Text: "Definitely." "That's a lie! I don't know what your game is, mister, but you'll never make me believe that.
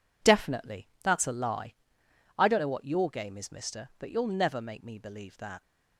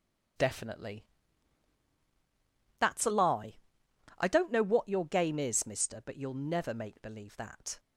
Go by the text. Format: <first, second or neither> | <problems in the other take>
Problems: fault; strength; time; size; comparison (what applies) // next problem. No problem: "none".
first | starts louder than the rest; strong; until 3.1 s; 7.5 dB // skips "me"; at 6.9 s